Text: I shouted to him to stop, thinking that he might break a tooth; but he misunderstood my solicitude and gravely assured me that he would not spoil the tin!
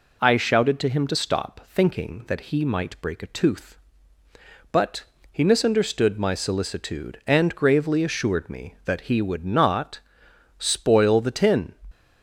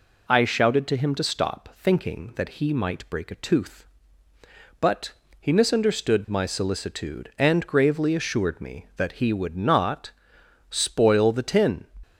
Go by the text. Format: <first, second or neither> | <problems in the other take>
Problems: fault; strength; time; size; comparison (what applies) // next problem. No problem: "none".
neither | pauses between "but" and "he"; slight; the same in both // pauses between "not" and "spoil"; noticeable; the same in both